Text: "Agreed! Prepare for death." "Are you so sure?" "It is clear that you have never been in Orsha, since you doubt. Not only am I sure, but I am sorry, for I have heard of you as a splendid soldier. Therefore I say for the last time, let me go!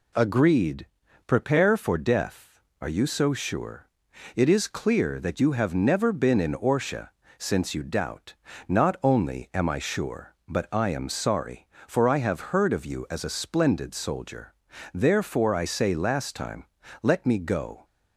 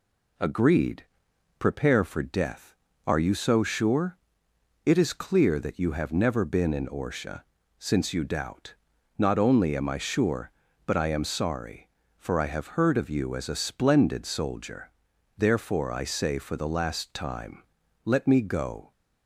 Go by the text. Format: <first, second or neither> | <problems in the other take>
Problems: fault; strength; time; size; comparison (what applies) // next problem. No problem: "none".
second | skips "for the"; at 15.9 s